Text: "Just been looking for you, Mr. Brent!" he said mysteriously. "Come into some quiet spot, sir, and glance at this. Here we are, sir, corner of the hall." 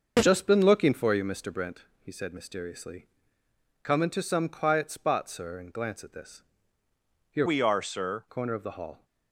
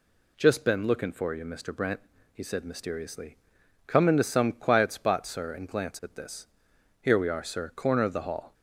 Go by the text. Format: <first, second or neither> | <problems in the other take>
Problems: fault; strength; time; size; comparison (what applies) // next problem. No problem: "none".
second | starts louder than the rest; noticeable; until 1.2 s; 6 dB // changes voice from "we" to "sir"; from 7.4 to 8.2 s; 0.8 s long